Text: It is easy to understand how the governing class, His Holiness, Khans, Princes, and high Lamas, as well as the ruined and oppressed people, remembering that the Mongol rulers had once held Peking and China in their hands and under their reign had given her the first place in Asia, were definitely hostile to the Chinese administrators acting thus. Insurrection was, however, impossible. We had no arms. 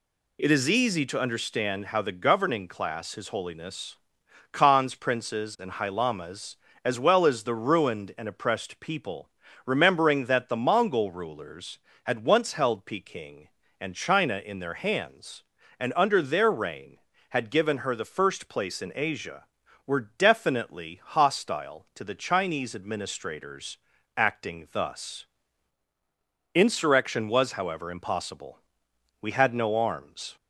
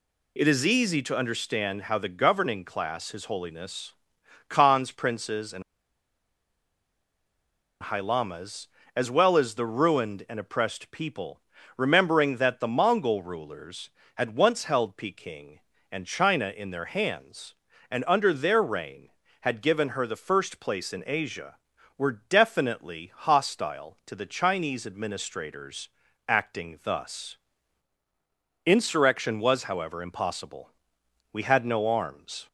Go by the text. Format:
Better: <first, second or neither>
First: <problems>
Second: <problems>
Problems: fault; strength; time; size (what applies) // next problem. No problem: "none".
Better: first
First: pauses between "administrators" and "acting"; at 23.7 s; 0.40 s long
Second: pauses between "and" and "high"; strong; at 5.6 s; 2.2 s long // pauses between "administrators" and "acting"; at 25.8 s; 0.40 s long